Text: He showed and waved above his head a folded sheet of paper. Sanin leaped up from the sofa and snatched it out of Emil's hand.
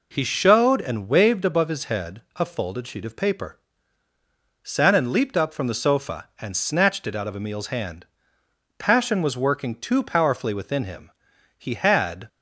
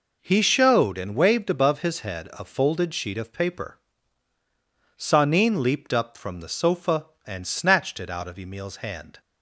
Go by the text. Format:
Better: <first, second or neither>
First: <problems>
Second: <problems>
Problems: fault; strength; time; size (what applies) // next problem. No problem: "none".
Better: second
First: pauses between "head" and "a"; slight; at 2.1 s; 0.16 s long // goes on to say "Passion was working too powerfully within him he had"; strong; from 8.7 s on; 3.5 s long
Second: none